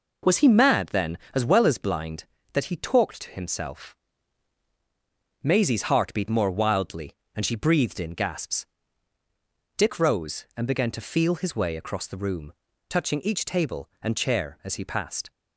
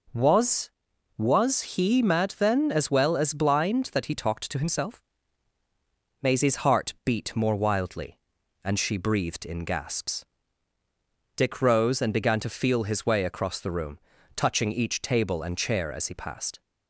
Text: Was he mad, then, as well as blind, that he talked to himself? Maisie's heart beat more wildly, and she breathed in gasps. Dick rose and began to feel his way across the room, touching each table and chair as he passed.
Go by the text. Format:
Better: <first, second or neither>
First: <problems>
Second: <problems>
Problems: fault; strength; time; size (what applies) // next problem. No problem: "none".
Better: first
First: none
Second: says "Was" twice; at 1.1 s